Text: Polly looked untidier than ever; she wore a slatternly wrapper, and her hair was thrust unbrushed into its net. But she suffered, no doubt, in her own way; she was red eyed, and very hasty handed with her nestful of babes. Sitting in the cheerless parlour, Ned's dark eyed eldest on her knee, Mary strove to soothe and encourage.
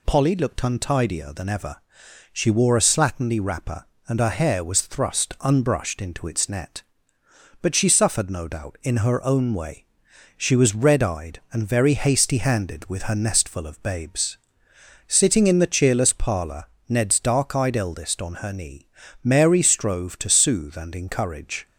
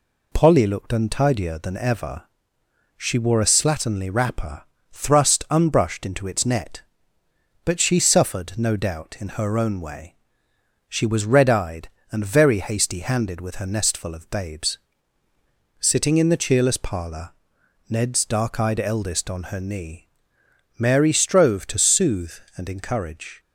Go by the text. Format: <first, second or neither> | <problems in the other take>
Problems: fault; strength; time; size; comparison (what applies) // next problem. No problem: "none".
first | skips "and her hair was"; at 4.7 s